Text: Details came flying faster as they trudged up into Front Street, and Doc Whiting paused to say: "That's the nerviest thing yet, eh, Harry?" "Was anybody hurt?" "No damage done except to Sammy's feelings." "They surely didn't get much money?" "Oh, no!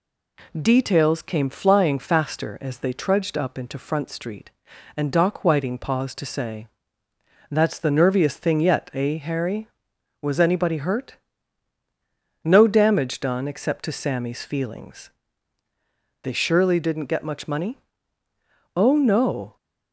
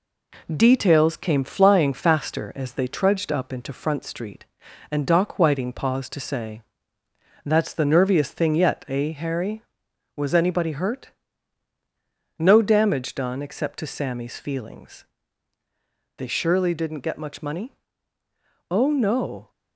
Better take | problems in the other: first | gets quieter; slight; throughout; 3 dB

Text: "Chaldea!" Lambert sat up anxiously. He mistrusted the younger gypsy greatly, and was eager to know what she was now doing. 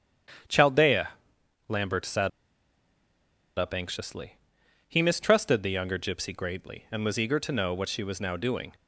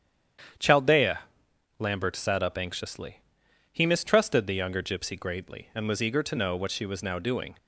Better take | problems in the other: second | starts louder than the rest; strong; until 2.0 s; 9 dB; strong in the second // pauses between "sat" and "up"; strong; at 2.2 s; 1.2 s long

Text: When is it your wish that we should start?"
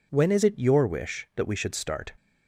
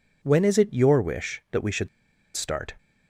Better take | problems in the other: first | pauses between "should" and "start"; noticeable; at 1.8 s; 0.48 s long

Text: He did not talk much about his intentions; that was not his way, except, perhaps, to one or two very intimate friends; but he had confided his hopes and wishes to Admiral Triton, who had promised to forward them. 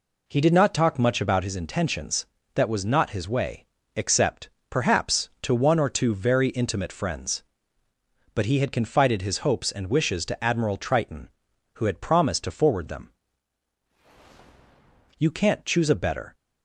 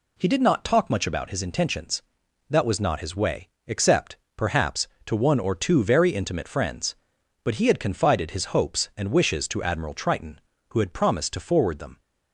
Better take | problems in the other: second | goes on to say "You can't choose a better"; noticeable; from 15.1 s on; 1.1 s long

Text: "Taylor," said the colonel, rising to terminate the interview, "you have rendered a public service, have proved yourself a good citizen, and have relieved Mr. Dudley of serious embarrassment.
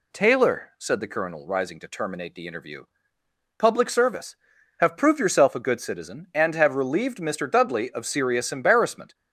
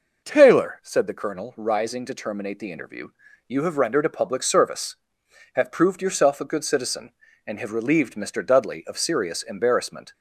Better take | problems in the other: second | skips "you have rendered a"; at 3.1 s

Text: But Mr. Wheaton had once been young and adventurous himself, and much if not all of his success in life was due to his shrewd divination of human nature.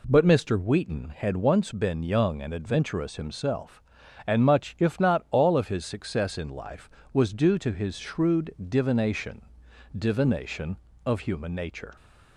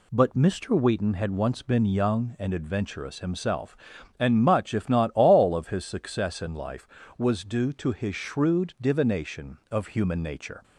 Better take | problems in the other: second | pauses between "shrewd" and "divination"; slight; at 8.5 s; 0.16 s long // says "divination" twice; at 9.9 s

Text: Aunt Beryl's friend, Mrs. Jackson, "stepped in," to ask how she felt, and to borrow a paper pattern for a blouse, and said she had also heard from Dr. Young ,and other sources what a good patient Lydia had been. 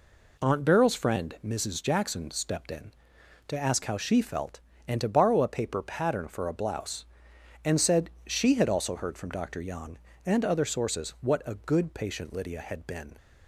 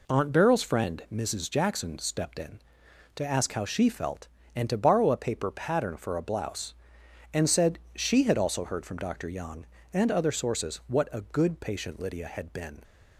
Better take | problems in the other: neither | pauses between "said" and "she"; slight; the same in both

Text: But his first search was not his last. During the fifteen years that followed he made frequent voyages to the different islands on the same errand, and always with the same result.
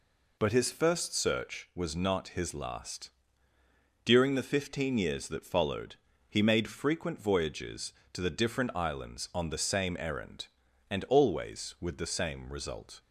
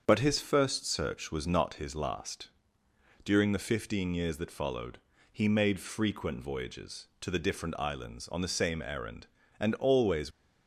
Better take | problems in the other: first | starts louder than the rest; until 1.0 s; 7 dB // pauses between "followed" and "he"; slight; at 4.9 s; 0.34 s long; slight in the first // stops before "with the same result"; at 10.3 s

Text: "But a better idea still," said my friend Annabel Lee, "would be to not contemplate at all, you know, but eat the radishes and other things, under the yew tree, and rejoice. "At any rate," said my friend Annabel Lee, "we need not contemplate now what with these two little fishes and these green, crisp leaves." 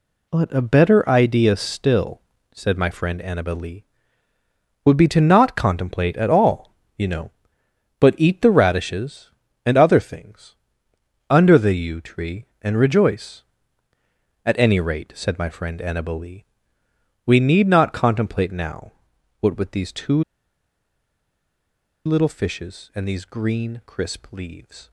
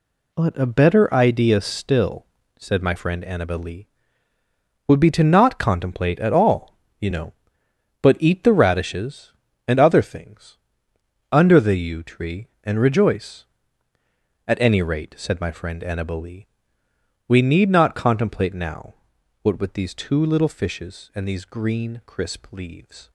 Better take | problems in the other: second | pauses between "now" and "what"; noticeable; at 18.9 s; 0.48 s long; noticeable in the second // pauses between "two" and "little"; strong; at 20.2 s; 1.8 s long

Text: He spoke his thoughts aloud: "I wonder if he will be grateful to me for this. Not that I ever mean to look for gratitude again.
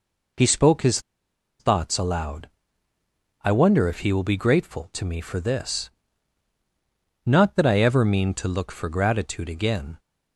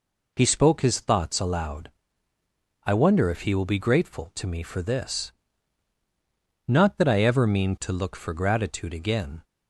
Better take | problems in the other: second | pauses between "his" and "thoughts"; noticeable; at 0.9 s; 0.59 s long

